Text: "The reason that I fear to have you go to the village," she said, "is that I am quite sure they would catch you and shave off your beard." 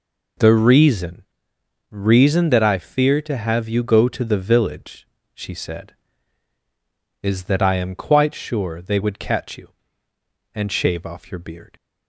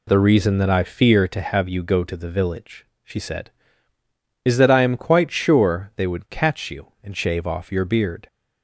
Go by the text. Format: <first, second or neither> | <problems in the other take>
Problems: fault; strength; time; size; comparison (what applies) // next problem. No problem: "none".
second | says "reason" twice; at 1.9 s